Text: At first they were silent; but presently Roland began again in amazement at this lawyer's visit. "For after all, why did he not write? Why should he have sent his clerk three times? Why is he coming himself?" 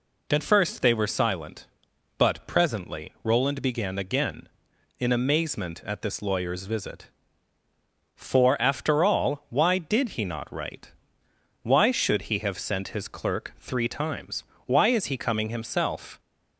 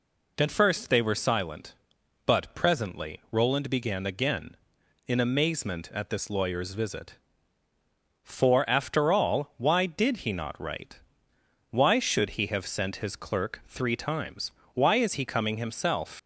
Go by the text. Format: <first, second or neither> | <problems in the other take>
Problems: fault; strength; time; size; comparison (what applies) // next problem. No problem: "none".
first | leaves "himself" unfinished; at 16.1 s; 75 ms